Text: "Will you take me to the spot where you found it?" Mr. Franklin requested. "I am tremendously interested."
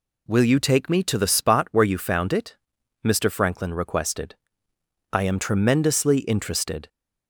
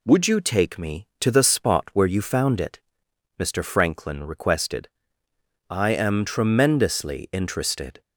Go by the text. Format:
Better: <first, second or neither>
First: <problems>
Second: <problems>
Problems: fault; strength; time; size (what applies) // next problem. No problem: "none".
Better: first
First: none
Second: says "Would" for "Will"; at 0.0 s